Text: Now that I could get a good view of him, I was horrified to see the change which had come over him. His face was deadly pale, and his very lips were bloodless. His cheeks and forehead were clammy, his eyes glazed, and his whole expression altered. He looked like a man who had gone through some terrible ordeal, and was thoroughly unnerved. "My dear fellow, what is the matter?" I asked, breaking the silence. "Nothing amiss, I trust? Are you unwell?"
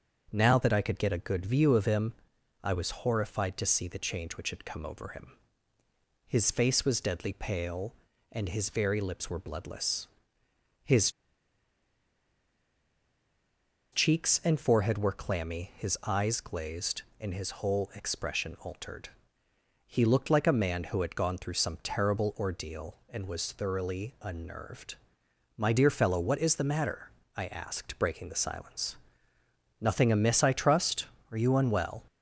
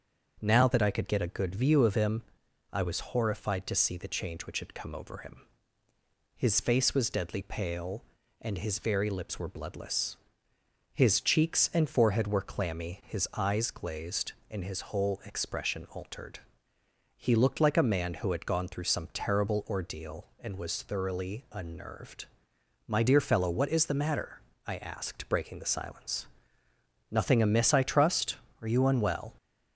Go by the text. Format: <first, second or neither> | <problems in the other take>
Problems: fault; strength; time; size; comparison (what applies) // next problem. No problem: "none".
second | starts louder than the rest; until 1.3 s; 6.5 dB; also in the second // pauses between "His" and "cheeks"; strong; at 11.0 s; 2.8 s long